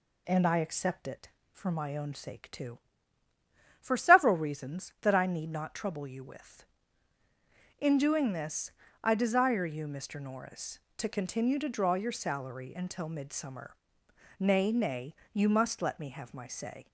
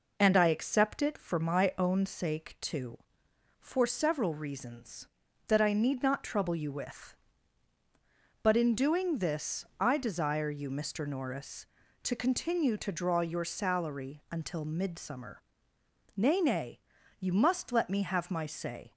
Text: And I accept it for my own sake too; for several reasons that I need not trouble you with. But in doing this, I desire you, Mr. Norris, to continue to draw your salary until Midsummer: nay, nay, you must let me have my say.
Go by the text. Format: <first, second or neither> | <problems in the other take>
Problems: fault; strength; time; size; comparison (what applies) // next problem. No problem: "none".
second | skips "But"; at 7.2 s